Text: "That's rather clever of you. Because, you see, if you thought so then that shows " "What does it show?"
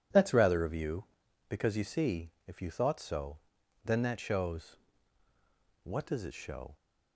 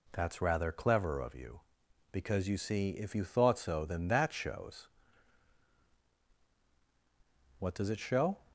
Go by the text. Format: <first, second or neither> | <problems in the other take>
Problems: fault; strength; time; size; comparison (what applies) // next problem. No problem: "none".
second | starts louder than the rest; strong; until 1.5 s; 11.5 dB // skips "clever"; at 0.6 s // pauses between "so" and "then"; noticeable; at 3.3 s; 0.46 s long